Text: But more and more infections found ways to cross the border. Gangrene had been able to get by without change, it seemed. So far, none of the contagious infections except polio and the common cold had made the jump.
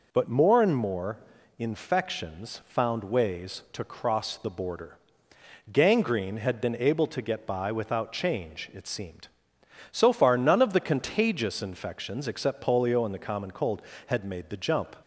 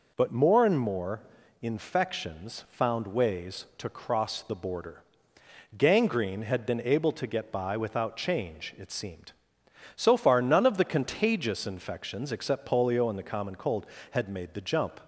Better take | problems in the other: neither | pauses between "more" and "infections"; the same in both

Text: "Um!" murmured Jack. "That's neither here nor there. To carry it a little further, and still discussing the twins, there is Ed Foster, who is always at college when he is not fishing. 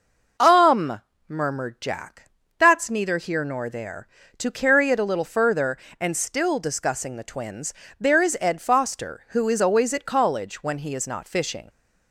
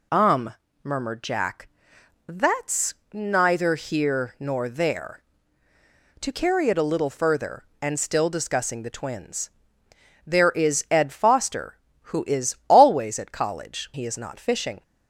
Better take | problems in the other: first | pauses between "That's" and "neither"; slight; at 2.9 s; 0.18 s long // skips "when"; at 13.9 s

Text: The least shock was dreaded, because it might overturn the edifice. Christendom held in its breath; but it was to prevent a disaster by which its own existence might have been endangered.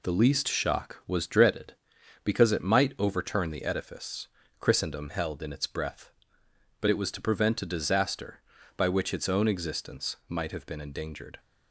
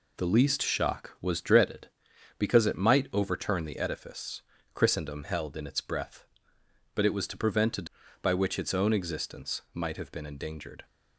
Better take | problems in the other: first | skips "disaster"; at 8.0 s

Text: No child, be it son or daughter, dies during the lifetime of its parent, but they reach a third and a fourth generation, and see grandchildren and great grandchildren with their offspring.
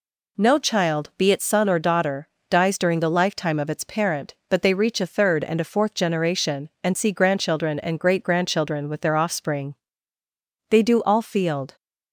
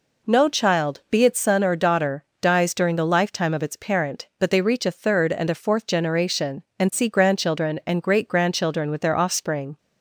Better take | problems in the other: second | goes on to say "They do all field"; noticeable; from 10.6 s on; 1.0 s long

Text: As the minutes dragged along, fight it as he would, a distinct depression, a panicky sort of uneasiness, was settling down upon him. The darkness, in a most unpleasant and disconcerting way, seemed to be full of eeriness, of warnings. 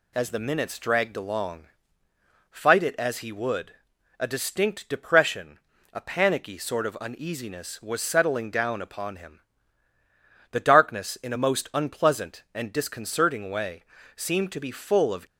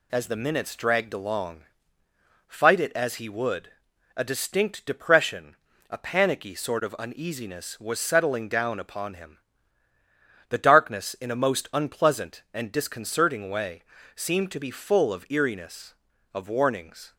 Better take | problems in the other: second | stops before "eeriness of warnings"; at 15.2 s

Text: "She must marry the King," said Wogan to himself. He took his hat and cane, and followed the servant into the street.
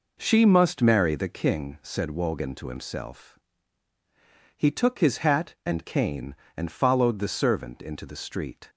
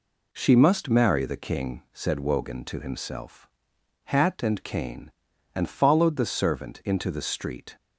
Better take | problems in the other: first | skips "He took his"; at 3.7 s

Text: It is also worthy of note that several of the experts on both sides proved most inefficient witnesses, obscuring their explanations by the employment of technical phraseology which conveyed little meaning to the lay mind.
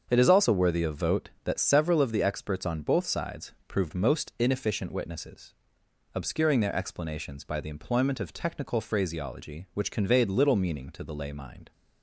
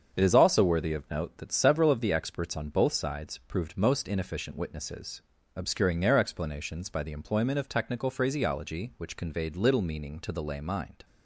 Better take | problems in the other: second | starts louder than the rest; until 1.0 s; 7 dB; also in the second // says "vote" for "note"; at 0.9 s

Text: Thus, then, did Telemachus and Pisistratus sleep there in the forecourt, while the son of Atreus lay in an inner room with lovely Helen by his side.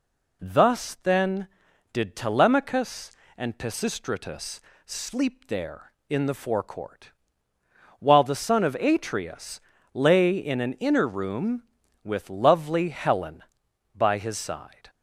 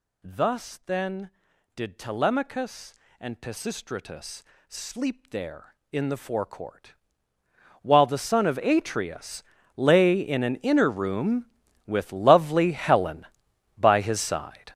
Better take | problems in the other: first | gets louder; strong; throughout; 11 dB // pauses between "Pisistratus" and "sleep"; slight; at 4.4 s; 0.26 s long; slight in the first // pauses between "Atreus" and "lay"; slight; at 9.4 s; 0.34 s long; slight in the first

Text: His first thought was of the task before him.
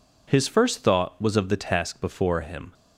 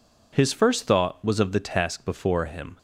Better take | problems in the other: neither | none

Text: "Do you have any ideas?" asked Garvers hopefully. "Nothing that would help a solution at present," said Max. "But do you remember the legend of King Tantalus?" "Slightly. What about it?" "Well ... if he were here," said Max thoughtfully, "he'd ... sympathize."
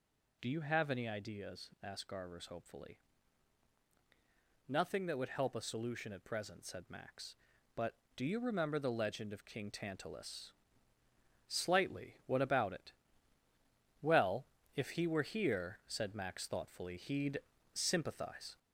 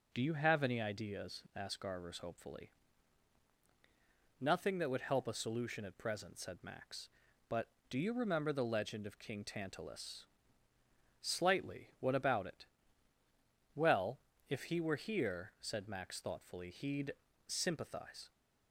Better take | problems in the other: second | gets louder; throughout; 3.5 dB

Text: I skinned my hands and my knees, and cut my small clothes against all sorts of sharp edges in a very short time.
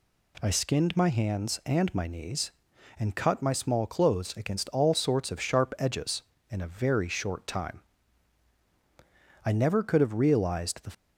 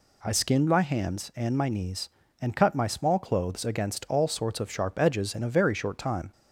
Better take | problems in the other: second | goes on to say "I never could have realized the"; from 9.4 s on; 1.3 s long

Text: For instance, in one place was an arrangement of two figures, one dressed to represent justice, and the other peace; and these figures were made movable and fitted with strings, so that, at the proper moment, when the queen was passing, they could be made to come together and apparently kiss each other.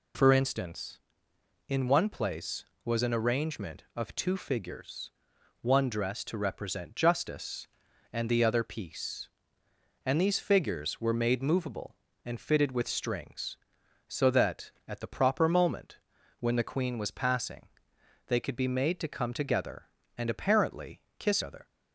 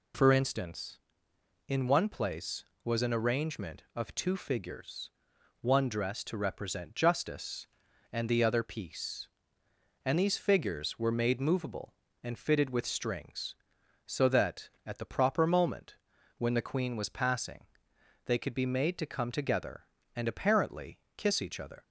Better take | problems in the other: second | pauses between "apparently" and "kiss"; slight; at 21.0 s; 0.16 s long; slight in the second // skips "each"; at 21.4 s

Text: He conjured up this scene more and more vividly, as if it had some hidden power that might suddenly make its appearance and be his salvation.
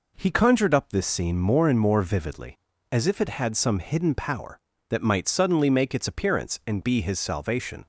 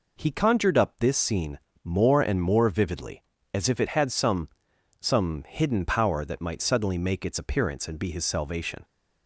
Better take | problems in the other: first | pauses between "scene" and "more"; slight; at 1.5 s; 0.24 s long // says "some" twice; at 4.9 s

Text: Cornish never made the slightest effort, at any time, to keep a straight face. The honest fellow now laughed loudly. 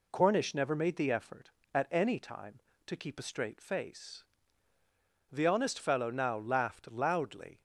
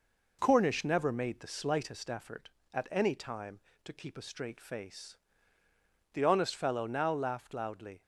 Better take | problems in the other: second | skips "slightest"; at 1.1 s

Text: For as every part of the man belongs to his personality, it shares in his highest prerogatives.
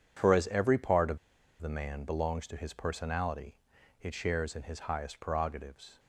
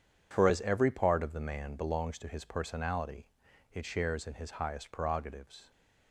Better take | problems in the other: second | pauses between "of" and "the"; at 1.1 s; 0.42 s long

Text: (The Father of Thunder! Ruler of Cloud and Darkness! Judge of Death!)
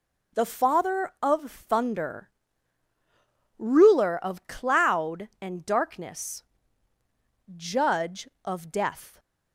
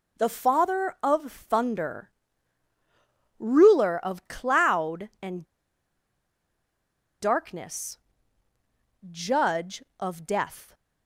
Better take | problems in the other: first | pauses between "and" and "Darkness"; strong; at 5.4 s; 1.7 s long

